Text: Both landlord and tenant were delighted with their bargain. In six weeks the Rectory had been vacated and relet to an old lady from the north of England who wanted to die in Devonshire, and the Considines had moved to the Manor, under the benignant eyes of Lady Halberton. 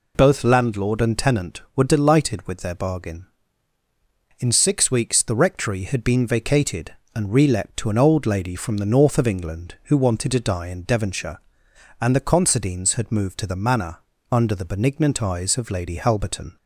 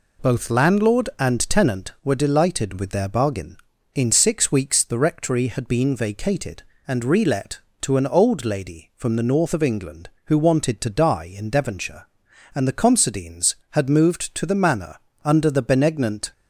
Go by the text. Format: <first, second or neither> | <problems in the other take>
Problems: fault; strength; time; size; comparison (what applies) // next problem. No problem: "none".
first | stops before "eyes of Lady Halberton"; at 16.3 s